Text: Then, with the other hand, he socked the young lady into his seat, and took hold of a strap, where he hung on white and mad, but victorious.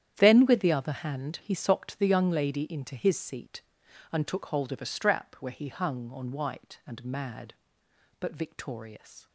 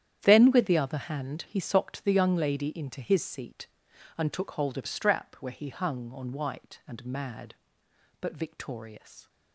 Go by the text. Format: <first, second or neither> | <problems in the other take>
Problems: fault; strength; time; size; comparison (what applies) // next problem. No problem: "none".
first | starts louder than the rest; strong; until 1.2 s; 10 dB; strong in the first // skips "a"; at 4.8 s